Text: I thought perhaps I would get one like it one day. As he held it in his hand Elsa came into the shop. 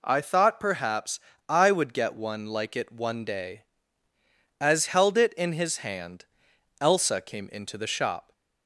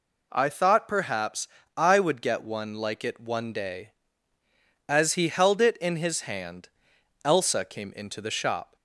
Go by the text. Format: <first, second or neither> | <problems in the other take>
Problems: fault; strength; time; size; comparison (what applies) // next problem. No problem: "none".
second | pauses between "perhaps" and "I"; slight; at 1.1 s; 0.30 s long; slight in the second // skips "he"; at 4.8 s // pauses between "hand" and "Elsa"; noticeable; at 6.2 s; 0.56 s long; noticeable in the second